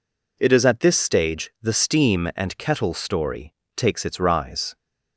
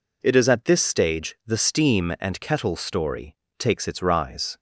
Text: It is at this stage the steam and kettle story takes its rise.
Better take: neither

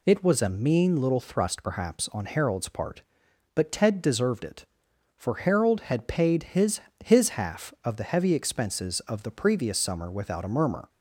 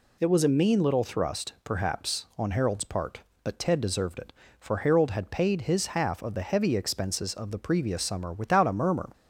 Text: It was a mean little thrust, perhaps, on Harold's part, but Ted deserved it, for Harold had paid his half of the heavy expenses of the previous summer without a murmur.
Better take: second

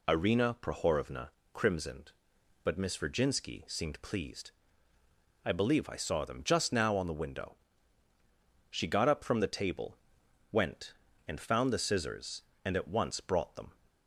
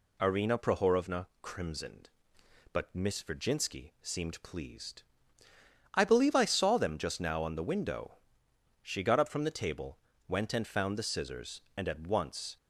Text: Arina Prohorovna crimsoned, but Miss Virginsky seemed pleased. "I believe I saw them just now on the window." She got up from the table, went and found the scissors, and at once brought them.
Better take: first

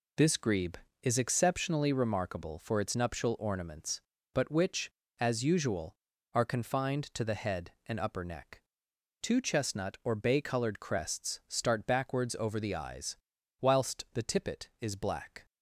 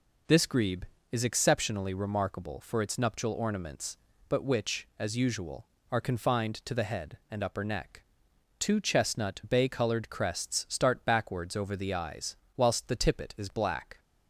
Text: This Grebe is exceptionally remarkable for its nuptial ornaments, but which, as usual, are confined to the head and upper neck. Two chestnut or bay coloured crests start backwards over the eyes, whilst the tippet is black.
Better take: first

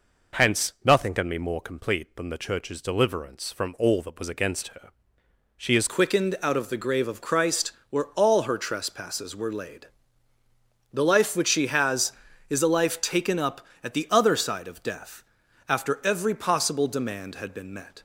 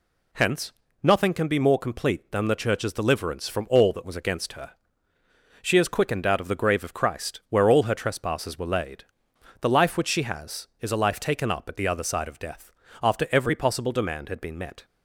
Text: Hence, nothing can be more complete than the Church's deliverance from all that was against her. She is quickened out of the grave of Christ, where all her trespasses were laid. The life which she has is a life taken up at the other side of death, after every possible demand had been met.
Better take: second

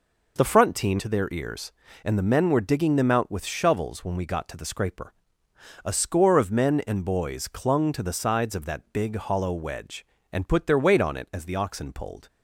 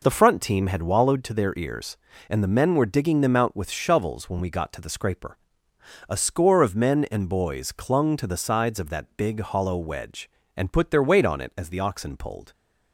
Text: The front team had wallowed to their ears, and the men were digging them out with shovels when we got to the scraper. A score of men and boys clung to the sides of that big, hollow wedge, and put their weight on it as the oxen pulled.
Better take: second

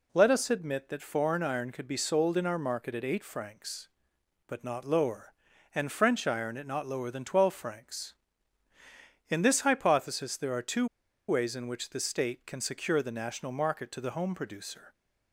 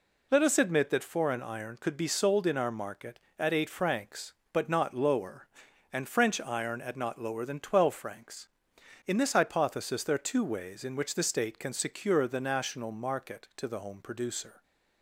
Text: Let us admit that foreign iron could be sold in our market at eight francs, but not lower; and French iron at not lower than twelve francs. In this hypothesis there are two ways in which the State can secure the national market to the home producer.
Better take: second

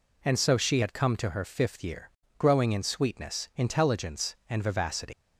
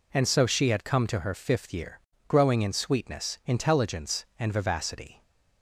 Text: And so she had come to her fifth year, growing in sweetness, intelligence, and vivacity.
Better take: second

